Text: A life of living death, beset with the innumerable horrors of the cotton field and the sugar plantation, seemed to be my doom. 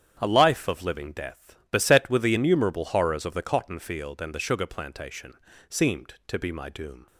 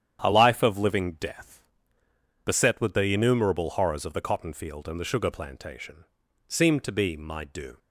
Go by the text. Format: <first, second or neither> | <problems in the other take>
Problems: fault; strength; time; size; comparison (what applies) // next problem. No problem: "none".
neither | starts louder than the rest; strong; the same in both